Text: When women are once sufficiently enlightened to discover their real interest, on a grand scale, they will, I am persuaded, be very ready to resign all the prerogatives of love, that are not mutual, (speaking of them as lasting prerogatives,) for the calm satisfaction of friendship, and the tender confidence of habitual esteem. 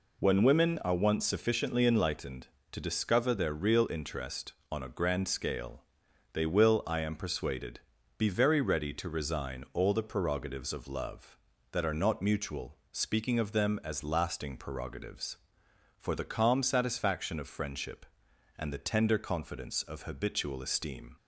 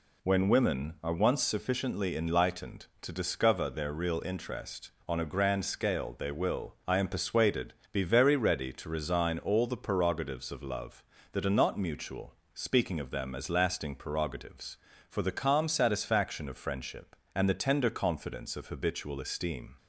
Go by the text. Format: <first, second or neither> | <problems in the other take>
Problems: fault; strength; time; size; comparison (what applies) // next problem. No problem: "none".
neither | none